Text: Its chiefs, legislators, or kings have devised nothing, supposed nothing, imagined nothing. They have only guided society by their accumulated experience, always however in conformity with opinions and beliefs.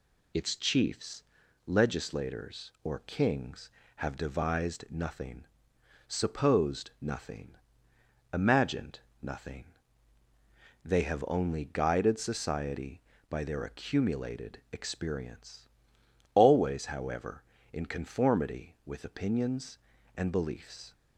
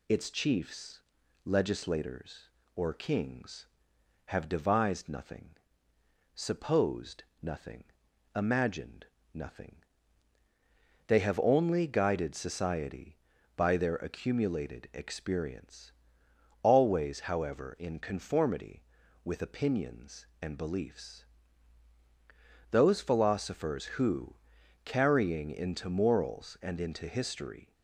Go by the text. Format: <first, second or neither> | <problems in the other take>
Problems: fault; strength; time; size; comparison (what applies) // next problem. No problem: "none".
first | pauses between "supposed" and "nothing"; slight; at 7.2 s; 0.18 s long // pauses between "imagined" and "nothing"; slight; at 9.0 s; 0.26 s long; slight in the first // goes on to say "Those philosophers who carrying into morals and into history"; strong; from 22.7 s on; 5.0 s long